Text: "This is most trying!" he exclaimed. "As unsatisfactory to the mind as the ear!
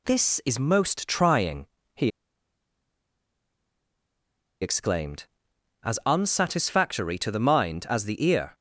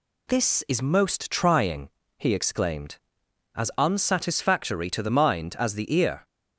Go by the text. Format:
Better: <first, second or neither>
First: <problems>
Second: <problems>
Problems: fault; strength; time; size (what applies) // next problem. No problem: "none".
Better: second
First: pauses between "he" and "exclaimed"; strong; at 2.1 s; 2.5 s long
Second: none